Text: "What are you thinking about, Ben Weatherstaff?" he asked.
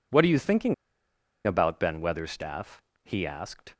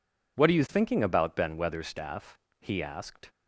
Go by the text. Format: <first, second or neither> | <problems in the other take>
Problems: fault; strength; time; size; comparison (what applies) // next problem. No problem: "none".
second | pauses between "thinking" and "about"; noticeable; at 0.7 s; 0.71 s long